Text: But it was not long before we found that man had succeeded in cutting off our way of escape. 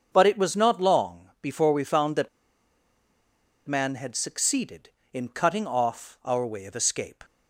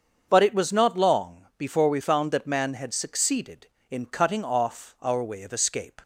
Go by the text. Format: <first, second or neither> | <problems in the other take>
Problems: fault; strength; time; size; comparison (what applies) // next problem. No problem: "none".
second | starts louder than the rest; until 1.1 s; 7 dB; also in the second // pauses between "that" and "man"; strong; at 2.2 s; 1.3 s long